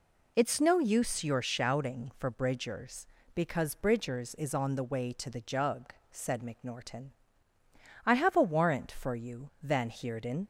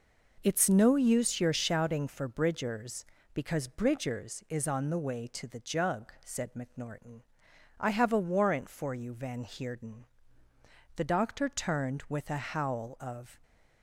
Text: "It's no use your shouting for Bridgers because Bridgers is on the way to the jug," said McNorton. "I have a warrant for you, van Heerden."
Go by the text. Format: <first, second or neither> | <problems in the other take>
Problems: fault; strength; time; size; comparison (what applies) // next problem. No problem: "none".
first | goes on to say "The doctor turned with a howl of"; strong; from 10.9 s on; 2.4 s long